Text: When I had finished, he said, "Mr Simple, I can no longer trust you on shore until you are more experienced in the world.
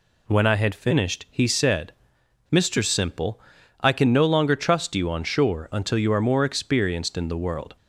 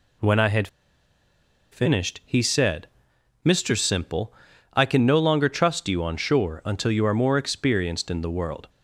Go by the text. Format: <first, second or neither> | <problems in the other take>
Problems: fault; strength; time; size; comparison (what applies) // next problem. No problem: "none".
first | pauses between "had" and "finished"; at 0.6 s; 1.0 s long